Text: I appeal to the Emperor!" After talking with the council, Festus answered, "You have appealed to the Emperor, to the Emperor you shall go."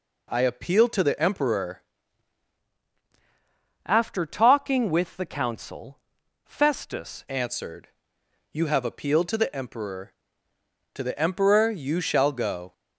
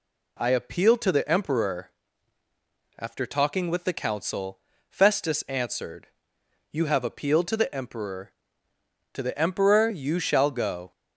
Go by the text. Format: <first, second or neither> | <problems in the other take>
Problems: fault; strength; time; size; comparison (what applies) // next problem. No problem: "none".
second | changes voice from "After" to "Festus"; from 3.8 to 7.2 s; 3.4 s long